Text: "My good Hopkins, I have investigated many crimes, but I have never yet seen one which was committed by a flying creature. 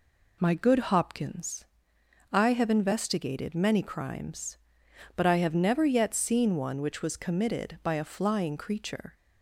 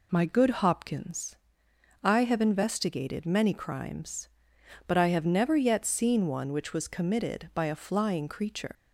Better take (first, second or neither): first